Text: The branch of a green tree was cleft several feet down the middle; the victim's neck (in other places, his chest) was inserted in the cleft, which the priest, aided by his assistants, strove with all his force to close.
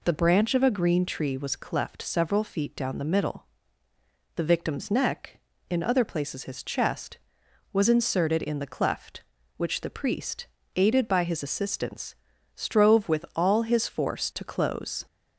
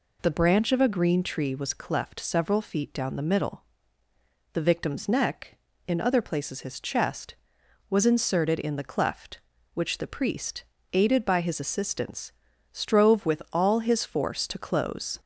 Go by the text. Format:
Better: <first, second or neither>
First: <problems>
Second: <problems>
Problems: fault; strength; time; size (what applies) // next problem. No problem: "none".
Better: neither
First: none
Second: none